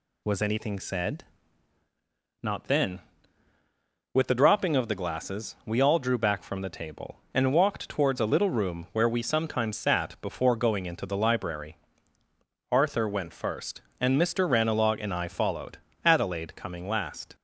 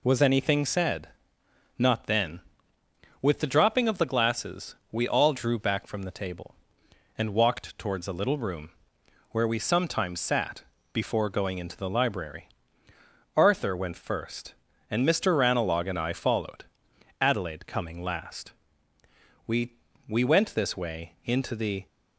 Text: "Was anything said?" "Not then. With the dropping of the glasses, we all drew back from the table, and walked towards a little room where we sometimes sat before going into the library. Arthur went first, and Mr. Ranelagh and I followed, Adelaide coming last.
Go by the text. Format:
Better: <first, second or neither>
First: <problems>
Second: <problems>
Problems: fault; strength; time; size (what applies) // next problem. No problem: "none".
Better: first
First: none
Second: pauses between "room" and "where"; noticeable; at 8.7 s; 0.58 s long // pauses between "sat" and "before"; slight; at 10.6 s; 0.28 s long // goes on to say "We we went this way into the"; strong; from 19.4 s on; 2.4 s long